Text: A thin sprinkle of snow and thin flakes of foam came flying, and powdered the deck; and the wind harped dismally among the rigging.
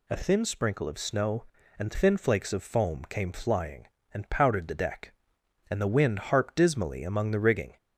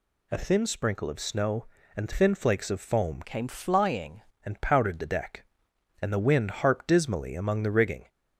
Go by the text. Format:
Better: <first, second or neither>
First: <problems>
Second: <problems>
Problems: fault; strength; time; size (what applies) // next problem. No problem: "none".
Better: first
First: none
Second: changes voice from "came" to "flying"; from 3.2 to 4.2 s; 1.0 s long